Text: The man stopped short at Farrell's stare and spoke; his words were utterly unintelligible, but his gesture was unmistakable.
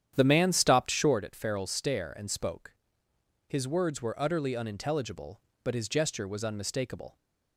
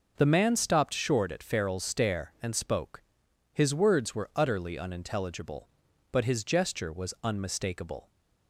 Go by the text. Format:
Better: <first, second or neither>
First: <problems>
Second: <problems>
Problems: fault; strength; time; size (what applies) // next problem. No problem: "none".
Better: second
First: starts louder than the rest; strong; until 1.2 s; 9.5 dB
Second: none